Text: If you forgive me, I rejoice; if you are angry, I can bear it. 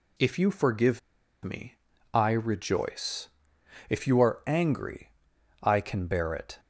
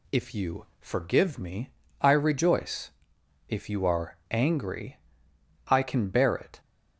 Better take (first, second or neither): second